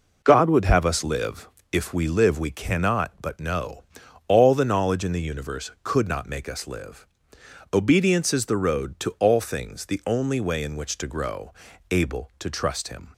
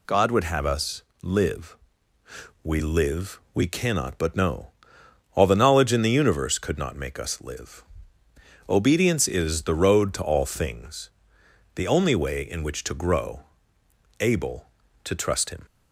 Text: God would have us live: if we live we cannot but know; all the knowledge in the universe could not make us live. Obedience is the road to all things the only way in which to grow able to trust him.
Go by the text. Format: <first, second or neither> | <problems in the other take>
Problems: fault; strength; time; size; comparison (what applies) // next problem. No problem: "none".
first | pauses between "us" and "live"; slight; at 1.0 s; 0.20 s long // skips "if"; at 2.1 s // pauses between "things" and "the"; noticeable; at 11.0 s; 0.66 s long // pauses between "grow" and "able"; noticeable; at 13.4 s; 0.78 s long; slight in the first